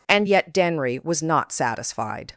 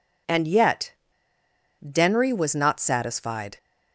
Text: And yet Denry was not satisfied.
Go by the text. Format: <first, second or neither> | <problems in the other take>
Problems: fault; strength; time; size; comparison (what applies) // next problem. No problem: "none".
first | pauses between "yet" and "Denry"; noticeable; at 0.9 s; 0.88 s long